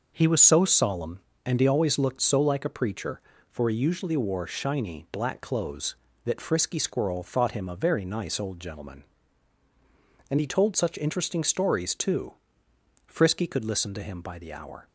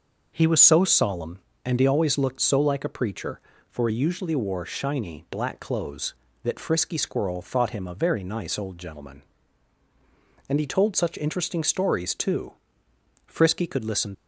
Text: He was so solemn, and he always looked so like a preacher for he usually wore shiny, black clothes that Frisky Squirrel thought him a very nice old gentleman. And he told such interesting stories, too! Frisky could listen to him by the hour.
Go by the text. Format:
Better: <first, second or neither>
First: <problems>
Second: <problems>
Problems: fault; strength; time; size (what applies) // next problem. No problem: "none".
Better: first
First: none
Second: stops before "to him by the hour"; at 14.1 s